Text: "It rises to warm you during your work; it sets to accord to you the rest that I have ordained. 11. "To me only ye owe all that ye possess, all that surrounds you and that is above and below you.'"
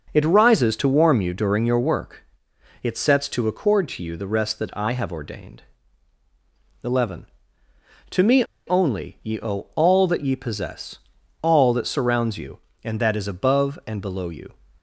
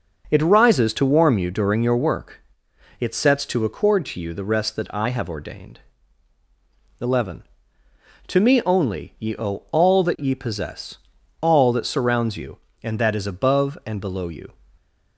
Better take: second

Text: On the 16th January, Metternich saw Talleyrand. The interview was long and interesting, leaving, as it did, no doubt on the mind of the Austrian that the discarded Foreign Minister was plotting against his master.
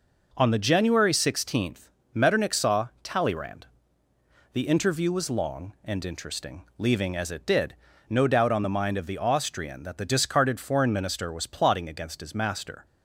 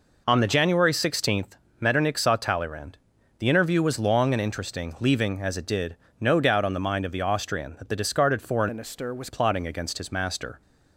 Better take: first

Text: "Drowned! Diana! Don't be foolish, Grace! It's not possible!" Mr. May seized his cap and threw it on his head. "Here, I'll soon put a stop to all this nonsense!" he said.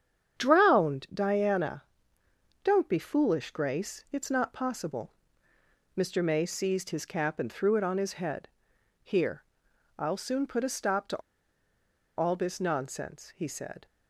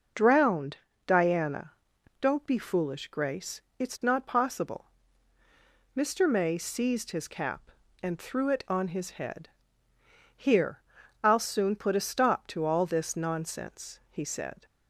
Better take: second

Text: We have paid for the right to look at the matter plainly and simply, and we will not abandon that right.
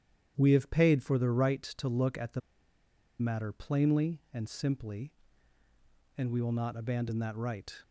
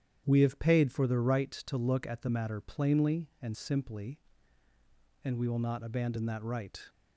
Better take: second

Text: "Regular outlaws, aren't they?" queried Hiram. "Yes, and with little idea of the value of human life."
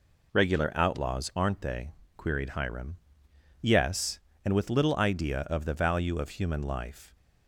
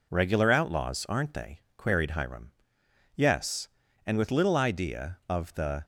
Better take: first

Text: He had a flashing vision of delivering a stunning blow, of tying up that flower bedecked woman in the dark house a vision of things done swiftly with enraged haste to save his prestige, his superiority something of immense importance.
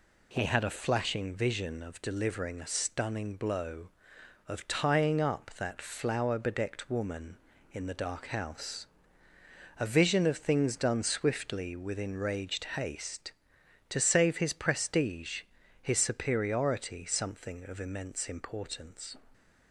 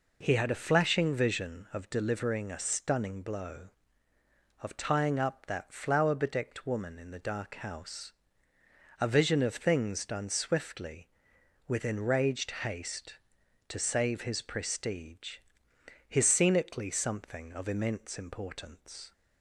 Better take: first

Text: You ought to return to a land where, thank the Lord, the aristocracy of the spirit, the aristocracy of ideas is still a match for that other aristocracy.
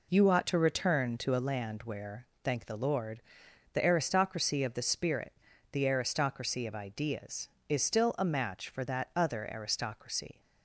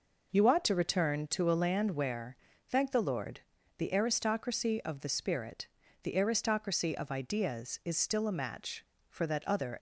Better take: first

